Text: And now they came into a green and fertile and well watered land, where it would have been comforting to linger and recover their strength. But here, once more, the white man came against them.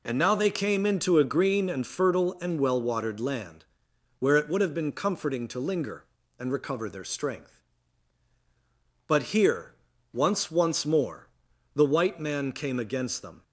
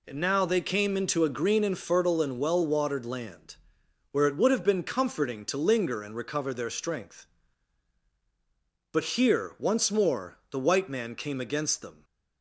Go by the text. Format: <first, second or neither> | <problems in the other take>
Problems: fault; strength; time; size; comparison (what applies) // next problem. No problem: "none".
second | says "once" twice; at 10.5 s